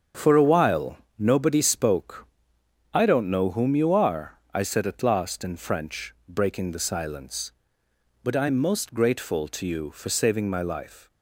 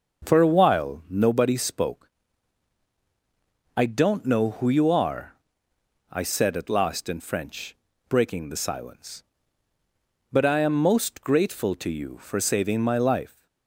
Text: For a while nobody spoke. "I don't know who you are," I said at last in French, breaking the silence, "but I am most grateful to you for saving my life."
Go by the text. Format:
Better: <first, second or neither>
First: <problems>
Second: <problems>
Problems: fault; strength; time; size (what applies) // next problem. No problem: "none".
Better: second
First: starts louder than the rest; strong; until 1.3 s; 7.5 dB // pauses between "while" and "nobody"; slight; at 0.9 s; 0.22 s long // says "whom" for "who"; at 3.4 s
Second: starts louder than the rest; until 1.3 s; 6.5 dB